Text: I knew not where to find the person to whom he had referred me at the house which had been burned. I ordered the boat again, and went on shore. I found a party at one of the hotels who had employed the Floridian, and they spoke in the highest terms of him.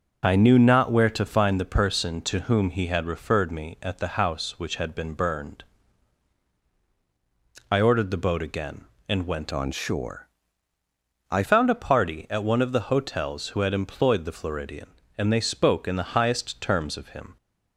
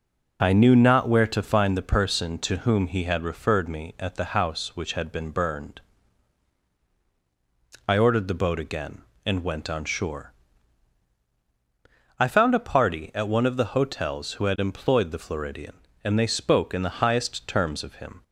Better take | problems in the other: second | changes voice from "on" to "I"; from 9.5 to 11.4 s; 1.9 s long

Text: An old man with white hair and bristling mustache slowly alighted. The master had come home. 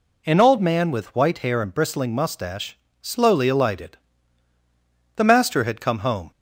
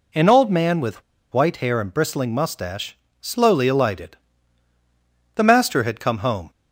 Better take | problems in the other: first | pauses between "with" and "white"; slight; at 1.0 s; 0.29 s long // pauses between "mustache" and "slowly"; slight; at 2.9 s; 0.24 s long; slight in the first

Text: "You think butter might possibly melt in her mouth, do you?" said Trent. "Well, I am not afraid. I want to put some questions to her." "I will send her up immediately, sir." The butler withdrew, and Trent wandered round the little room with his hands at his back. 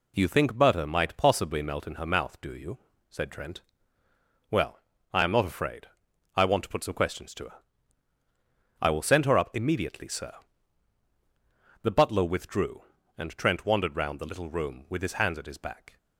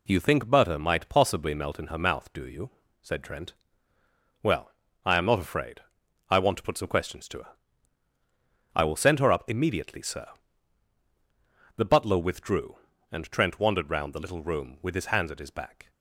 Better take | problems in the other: neither | none

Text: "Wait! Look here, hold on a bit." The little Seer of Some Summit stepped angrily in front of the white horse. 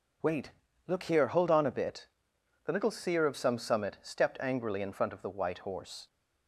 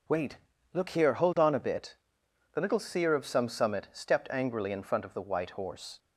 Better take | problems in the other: neither | none

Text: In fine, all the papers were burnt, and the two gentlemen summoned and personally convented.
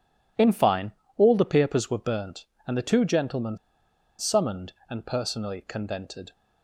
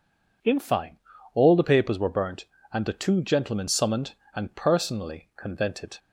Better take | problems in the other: second | pauses between "gentlemen" and "summoned"; noticeable; at 3.5 s; 0.61 s long

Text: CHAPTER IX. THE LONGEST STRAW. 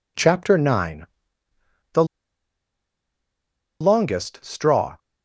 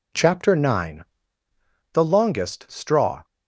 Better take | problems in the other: second | pauses between "THE" and "LONGEST"; strong; at 2.0 s; 1.7 s long

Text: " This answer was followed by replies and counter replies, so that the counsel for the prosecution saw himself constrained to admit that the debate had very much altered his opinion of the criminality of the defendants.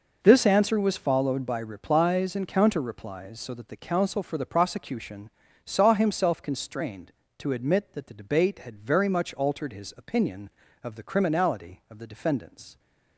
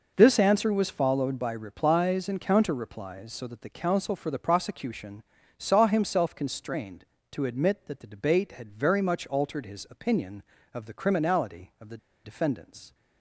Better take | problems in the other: first | pauses between "prosecution" and "saw"; slight; at 5.2 s; 0.34 s long; slight in the first // pauses between "the" and "defendants"; slight; at 11.9 s; 0.27 s long

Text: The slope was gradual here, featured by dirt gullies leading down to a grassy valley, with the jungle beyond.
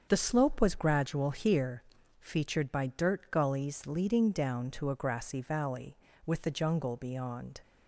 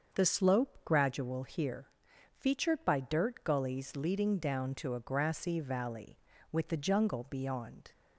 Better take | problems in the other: first | starts louder than the rest; until 1.2 s; 6.5 dB; also in the first // skips "was"; at 0.7 s

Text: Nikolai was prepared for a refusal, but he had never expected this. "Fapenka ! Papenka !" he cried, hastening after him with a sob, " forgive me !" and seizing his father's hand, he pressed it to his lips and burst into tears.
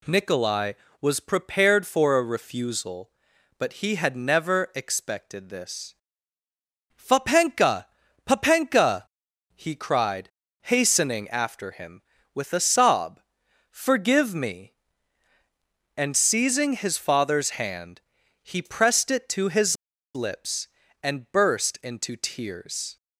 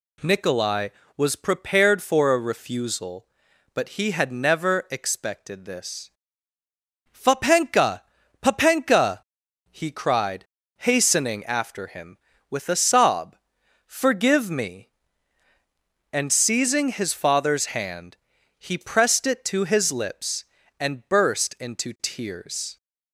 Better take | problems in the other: second | pauses between "his" and "lips"; at 19.7 s; 0.39 s long

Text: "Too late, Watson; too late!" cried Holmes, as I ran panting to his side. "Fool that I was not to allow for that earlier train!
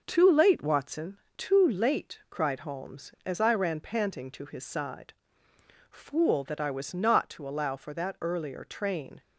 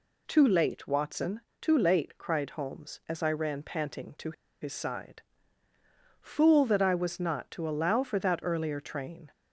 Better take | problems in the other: first | pauses between "to" and "his"; slight; at 4.3 s; 0.29 s long

